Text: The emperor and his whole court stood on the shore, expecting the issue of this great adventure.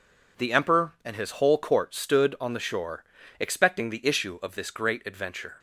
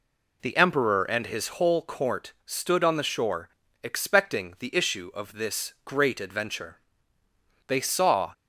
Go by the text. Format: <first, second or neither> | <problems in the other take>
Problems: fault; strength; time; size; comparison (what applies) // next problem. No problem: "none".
first | goes on to say "They saw"; noticeable; from 7.6 s on; 0.66 s long